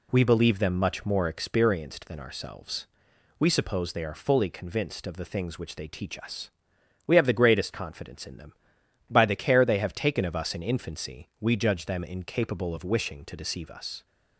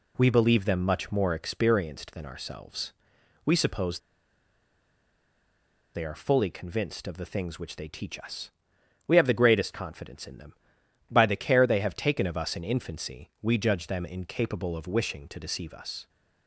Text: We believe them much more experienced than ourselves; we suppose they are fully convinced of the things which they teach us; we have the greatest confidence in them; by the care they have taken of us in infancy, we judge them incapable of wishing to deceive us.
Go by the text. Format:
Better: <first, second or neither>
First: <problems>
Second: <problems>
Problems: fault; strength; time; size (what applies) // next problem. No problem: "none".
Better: first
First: none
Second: pauses between "suppose" and "they"; strong; at 3.9 s; 1.9 s long